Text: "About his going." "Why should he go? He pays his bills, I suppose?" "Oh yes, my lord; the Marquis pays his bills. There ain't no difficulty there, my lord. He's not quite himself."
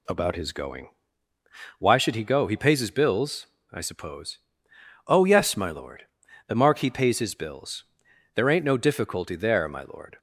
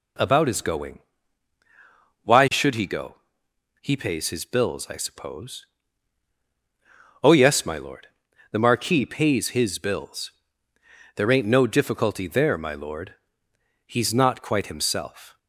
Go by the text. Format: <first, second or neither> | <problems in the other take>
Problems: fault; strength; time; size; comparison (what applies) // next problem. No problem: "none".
second | stops before "He's not quite himself"; at 10.1 s